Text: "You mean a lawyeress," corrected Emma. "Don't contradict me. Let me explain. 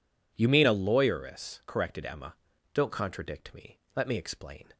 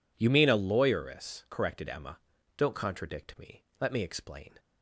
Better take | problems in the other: neither | none

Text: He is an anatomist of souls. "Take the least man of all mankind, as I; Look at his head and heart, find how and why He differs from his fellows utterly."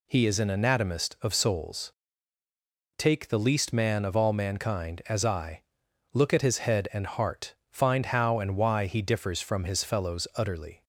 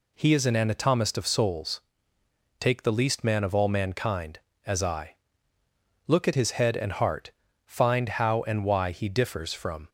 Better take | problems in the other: first | stops before "his fellows utterly"; at 9.8 s

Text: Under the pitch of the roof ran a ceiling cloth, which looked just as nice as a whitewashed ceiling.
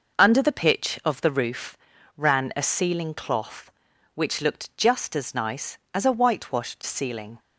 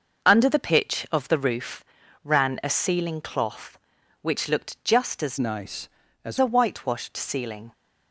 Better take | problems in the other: first | pauses between "roof" and "ran"; at 1.8 s; 0.40 s long; also in the first // changes voice from "nice" to "as"; from 5.3 to 6.3 s; 1.0 s long

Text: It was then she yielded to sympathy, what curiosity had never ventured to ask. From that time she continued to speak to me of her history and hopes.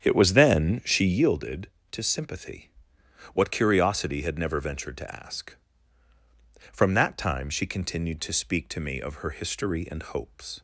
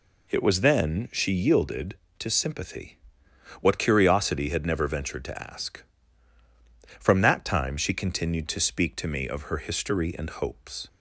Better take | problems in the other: second | starts louder than the rest; strong; until 1.3 s; 8.5 dB

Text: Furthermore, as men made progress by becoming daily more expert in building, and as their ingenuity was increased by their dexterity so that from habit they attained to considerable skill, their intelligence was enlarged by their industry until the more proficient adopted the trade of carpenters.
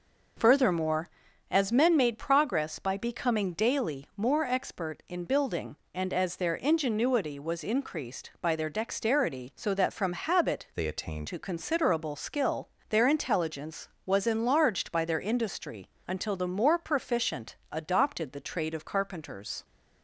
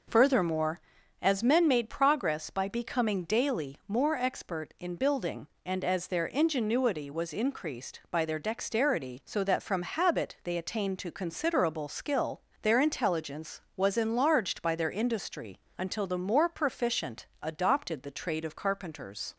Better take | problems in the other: second | changes voice from "they" to "attained"; from 10.7 to 11.2 s; 0.5 s long // pauses between "industry" and "until"; slight; at 15.8 s; 0.20 s long; slight in the second // pauses between "proficient" and "adopted"; slight; at 17.5 s; 0.16 s long; slight in the second

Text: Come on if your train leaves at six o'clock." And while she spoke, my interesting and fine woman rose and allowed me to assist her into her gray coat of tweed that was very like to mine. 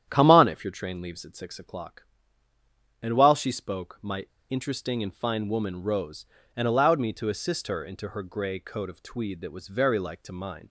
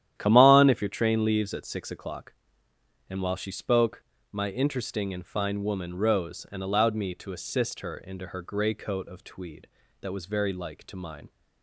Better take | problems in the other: second | starts louder than the rest; strong; until 1.0 s; 10 dB; strong in the second // pauses between "my" and "interesting"; slight; at 4.2 s; 0.25 s long

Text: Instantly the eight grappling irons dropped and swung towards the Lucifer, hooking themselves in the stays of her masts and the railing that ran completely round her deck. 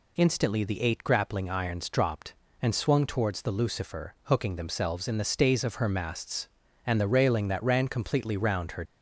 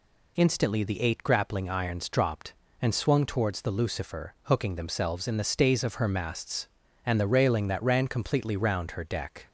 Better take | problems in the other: second | stops before "deck"; at 8.8 s

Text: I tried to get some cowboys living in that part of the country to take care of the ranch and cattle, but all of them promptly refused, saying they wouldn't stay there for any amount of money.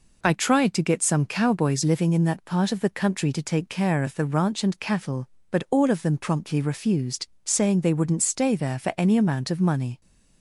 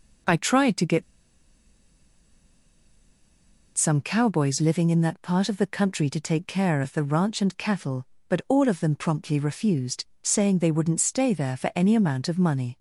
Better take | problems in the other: first | pauses between "get" and "some"; strong; at 1.0 s; 2.7 s long

